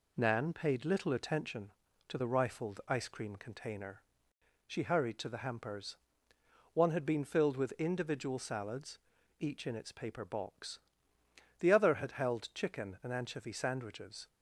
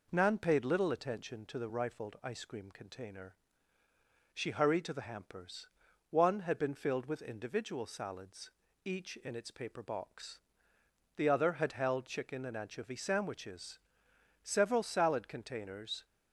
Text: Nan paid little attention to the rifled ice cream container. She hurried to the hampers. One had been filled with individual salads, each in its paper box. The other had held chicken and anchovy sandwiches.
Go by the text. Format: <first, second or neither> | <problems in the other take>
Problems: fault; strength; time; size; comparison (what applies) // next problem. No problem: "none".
first | goes on to say "Several salad containers"; from 14.4 s on; 1.6 s long